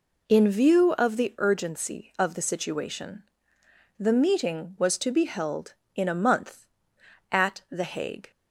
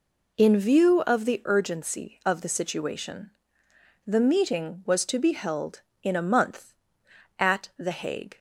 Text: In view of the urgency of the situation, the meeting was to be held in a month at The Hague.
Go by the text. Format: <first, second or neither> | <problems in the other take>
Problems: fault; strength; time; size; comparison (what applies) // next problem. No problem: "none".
neither | none